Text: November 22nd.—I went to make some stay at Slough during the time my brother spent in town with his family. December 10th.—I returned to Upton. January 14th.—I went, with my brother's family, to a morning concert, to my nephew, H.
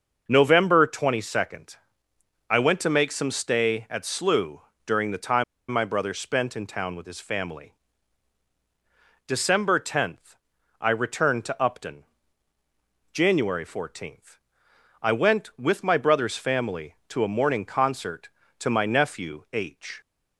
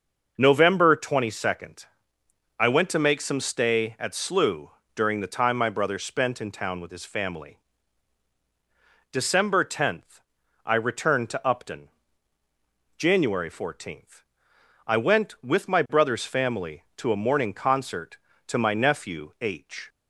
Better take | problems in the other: second | starts louder than the rest; noticeable; until 1.2 s; 6 dB; noticeable in the second // pauses between "Slough" and "during"; slight; at 4.6 s; 0.24 s long; slight in the second // pauses between "time" and "my"; slight; at 5.4 s; 0.26 s long

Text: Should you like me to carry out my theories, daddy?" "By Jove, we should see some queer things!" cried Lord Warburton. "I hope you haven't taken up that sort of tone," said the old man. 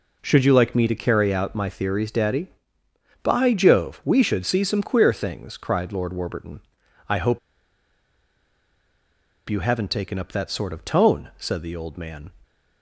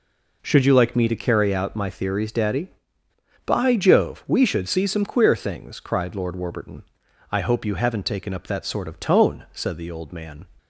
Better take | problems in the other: second | pauses between "hope" and "you"; strong; at 7.3 s; 2.0 s long

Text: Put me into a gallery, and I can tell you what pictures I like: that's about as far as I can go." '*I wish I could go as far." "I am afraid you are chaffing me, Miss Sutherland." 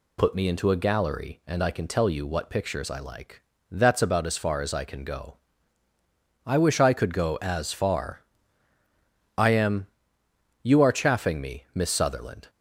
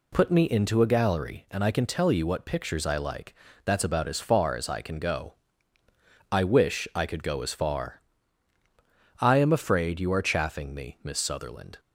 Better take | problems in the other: second | skips "afraid"; at 10.2 s

